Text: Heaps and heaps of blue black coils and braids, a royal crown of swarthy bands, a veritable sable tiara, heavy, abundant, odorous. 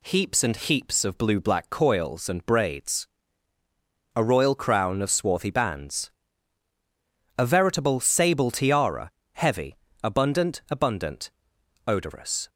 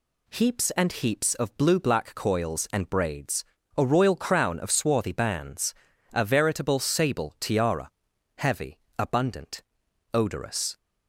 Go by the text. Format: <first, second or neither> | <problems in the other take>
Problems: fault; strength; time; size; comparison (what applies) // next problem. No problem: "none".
second | says "abundant" twice; at 10.6 s